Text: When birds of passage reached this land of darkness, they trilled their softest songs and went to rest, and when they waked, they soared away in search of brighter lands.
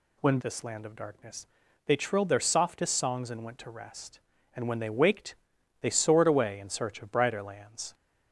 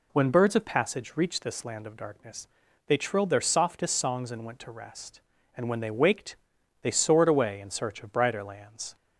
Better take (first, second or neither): second